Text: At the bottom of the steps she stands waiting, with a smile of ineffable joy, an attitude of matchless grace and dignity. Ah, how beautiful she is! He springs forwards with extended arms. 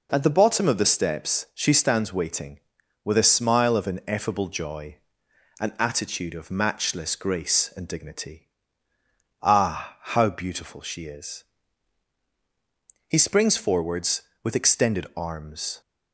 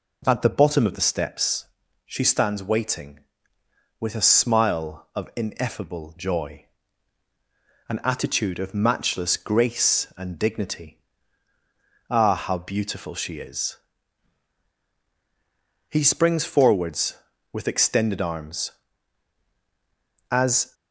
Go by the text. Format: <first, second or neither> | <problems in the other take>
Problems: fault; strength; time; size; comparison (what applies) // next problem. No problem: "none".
first | pauses between "steps" and "she"; at 1.6 s; 0.40 s long // goes on to say "As"; slight; from 20.3 s on; 0.42 s long